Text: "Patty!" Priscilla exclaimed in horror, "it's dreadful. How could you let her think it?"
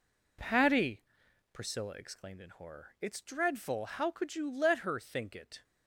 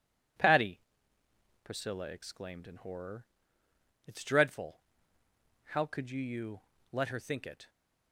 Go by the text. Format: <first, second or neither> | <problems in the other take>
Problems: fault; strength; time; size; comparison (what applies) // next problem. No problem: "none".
first | says "you" twice; at 6.2 s